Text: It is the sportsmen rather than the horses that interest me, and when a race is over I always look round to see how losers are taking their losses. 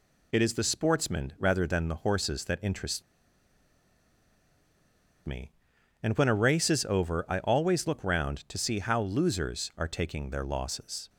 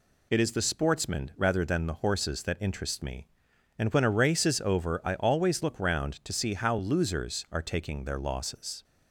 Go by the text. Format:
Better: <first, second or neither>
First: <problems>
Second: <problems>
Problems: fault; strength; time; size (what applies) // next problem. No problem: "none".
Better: second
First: pauses between "interest" and "me"; strong; at 3.0 s; 2.2 s long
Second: none